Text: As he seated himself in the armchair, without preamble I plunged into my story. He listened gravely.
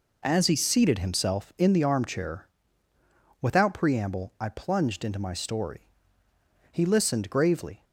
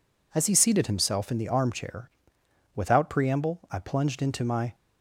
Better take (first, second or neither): first